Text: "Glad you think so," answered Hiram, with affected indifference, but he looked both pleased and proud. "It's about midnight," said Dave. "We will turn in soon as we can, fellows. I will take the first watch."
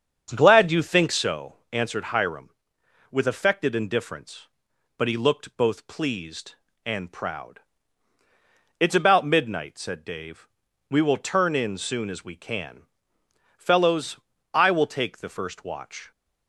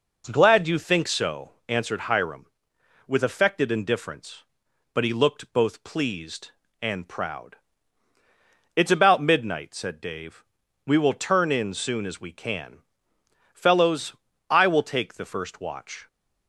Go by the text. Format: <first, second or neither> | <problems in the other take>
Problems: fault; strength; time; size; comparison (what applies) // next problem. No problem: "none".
second | starts louder than the rest; strong; until 1.3 s; 7.5 dB